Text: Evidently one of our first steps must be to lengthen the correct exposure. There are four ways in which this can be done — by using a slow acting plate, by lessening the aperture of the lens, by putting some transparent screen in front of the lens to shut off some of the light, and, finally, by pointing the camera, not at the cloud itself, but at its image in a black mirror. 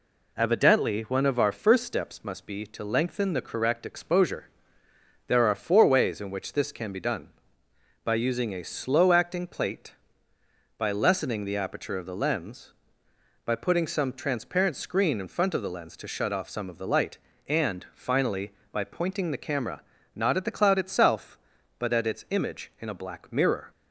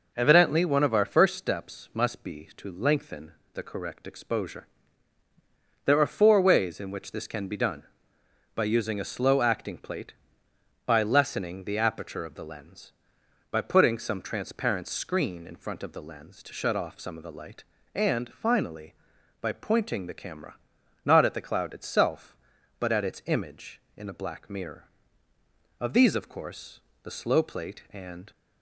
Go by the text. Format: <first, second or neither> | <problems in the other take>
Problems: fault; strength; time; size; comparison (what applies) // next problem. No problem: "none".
first | pauses between "lengthen" and "the"; slight; at 3.3 s; 0.24 s long // goes on to say "Of these of course the slow plate and"; strong; from 25.8 s on; 2.5 s long